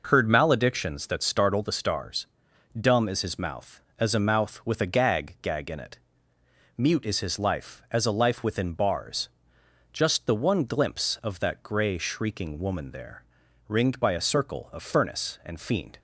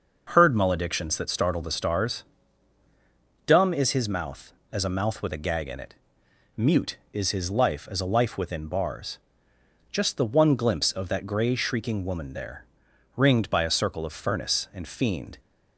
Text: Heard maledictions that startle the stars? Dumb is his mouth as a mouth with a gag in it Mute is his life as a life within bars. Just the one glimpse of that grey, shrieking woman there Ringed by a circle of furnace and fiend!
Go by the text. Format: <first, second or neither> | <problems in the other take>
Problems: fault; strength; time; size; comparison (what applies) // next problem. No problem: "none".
second | says "gag" twice; at 5.4 s // pauses between "it" and "Mute"; noticeable; at 5.9 s; 0.80 s long; noticeable in the second // pauses between "there" and "Ringed"; at 13.2 s; 0.44 s long; noticeable in the second